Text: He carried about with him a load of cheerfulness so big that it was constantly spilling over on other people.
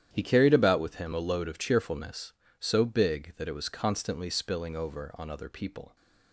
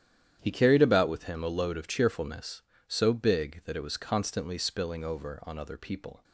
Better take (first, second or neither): neither